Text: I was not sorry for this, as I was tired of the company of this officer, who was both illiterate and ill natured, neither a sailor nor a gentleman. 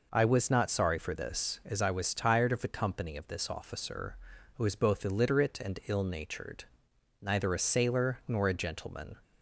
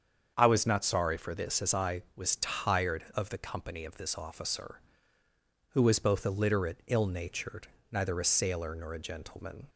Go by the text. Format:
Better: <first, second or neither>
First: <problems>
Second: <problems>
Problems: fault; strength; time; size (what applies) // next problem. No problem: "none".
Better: first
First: none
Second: starts louder than the rest; strong; until 1.3 s; 7.5 dB // skips "and"; at 6.8 s